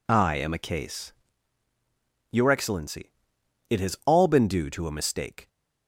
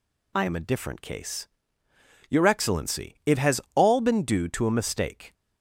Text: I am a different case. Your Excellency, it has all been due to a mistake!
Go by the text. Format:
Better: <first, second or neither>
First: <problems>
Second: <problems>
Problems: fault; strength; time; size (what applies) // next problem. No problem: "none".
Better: second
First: skips "different"; at 0.5 s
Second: none